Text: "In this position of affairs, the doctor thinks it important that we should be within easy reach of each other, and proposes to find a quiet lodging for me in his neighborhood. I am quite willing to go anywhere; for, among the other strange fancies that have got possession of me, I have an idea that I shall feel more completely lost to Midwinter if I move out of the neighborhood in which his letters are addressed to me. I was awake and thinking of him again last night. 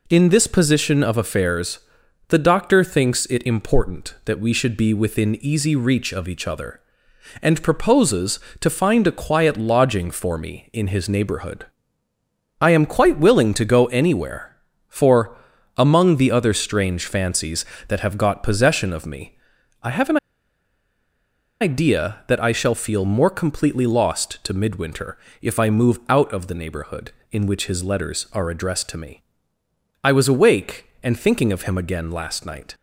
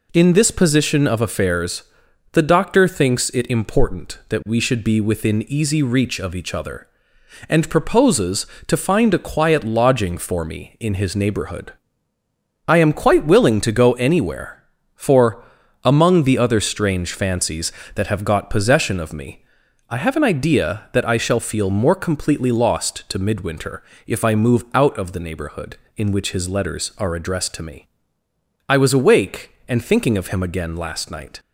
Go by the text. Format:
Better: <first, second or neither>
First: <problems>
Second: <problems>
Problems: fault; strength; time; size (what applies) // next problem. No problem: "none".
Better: second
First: pauses between "an" and "idea"; strong; at 20.1 s; 1.4 s long // pauses between "Midwinter" and "if"; slight; at 25.1 s; 0.24 s long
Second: pauses between "Midwinter" and "if"; slight; at 23.8 s; 0.24 s long